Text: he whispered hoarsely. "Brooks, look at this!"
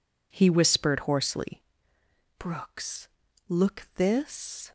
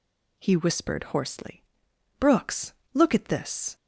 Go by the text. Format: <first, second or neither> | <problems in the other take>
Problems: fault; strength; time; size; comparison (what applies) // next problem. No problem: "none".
second | skips "at"; at 3.9 s